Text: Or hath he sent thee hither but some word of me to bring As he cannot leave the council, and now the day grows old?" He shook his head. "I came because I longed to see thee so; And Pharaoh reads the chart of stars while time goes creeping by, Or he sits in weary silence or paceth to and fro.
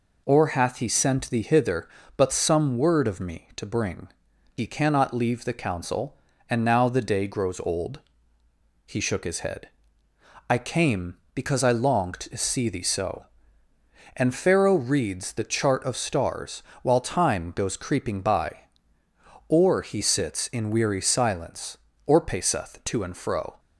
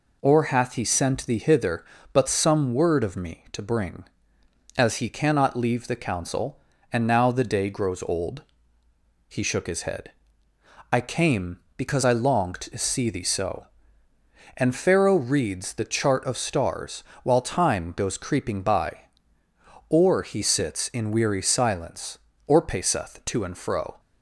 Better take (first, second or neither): second